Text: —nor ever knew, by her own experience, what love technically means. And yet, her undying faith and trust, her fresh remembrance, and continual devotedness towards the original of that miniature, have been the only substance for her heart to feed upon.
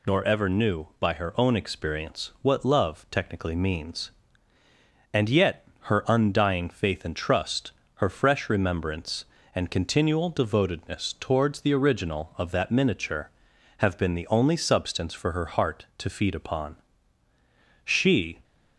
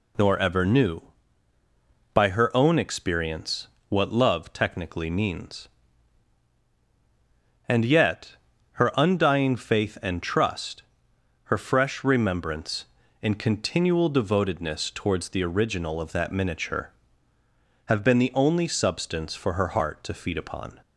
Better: second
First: goes on to say "She"; from 17.8 s on; 0.58 s long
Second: none

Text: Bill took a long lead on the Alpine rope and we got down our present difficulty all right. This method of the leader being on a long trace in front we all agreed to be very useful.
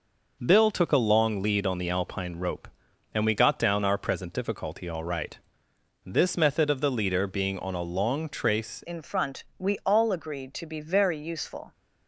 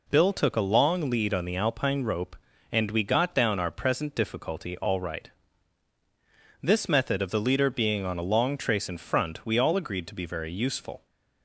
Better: second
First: changes voice at "in"; from 8.8 s on; 2.9 s long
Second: none

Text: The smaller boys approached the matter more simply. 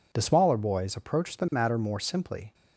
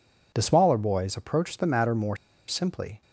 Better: first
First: none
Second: pauses between "more" and "simply"; slight; at 2.1 s; 0.31 s long

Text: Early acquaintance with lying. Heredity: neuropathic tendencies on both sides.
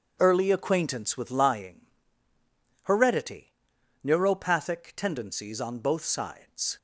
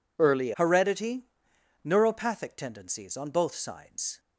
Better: first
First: none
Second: skips "acquaintance with lying"; at 0.5 s

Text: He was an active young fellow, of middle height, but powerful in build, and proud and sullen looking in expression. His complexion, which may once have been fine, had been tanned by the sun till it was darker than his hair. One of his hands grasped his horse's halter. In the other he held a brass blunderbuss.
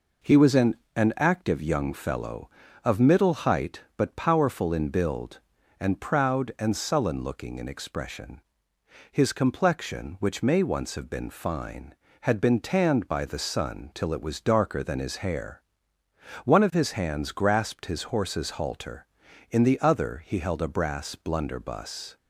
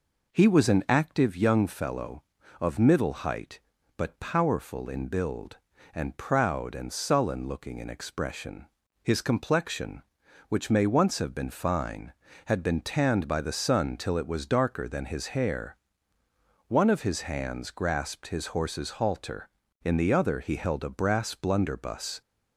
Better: second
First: says "an" twice; at 0.9 s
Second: none

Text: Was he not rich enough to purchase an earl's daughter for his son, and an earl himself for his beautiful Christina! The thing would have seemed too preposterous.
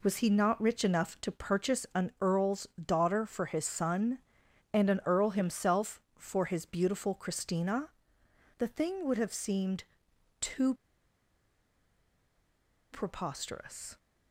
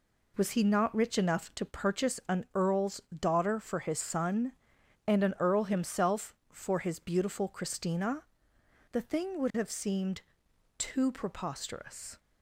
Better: second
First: pauses between "earl's" and "daughter"; slight; at 2.6 s; 0.16 s long // pauses between "seemed" and "too"; noticeable; at 9.8 s; 0.56 s long // pauses between "too" and "preposterous"; strong; at 10.7 s; 2.1 s long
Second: pauses between "earl's" and "daughter"; slight; at 3.0 s; 0.16 s long // pauses between "seemed" and "too"; noticeable; at 10.2 s; 0.56 s long

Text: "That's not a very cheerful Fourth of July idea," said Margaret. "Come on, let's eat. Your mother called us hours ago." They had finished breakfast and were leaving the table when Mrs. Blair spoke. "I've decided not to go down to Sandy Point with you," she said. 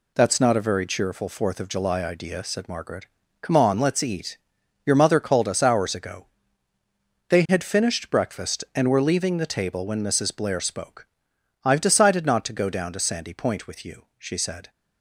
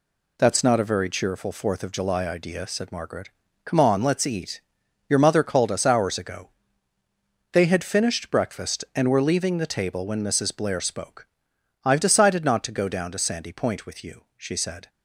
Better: neither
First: none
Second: none

